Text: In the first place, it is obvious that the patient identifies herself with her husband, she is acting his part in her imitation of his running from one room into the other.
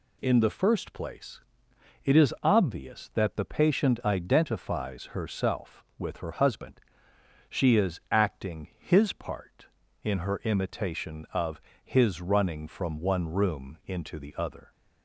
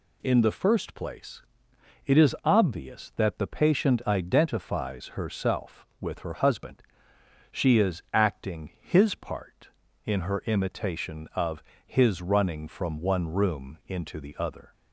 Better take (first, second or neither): neither